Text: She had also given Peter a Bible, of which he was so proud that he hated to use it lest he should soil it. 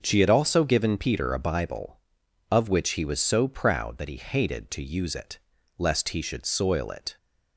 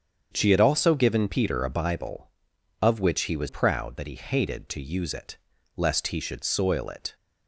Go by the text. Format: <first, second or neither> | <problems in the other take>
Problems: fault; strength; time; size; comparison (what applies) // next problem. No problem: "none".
first | starts louder than the rest; strong; until 1.3 s; 7.5 dB; also in the first // skips "so"; at 3.4 s // pauses between "it" and "lest"; at 5.3 s; 0.38 s long; also in the first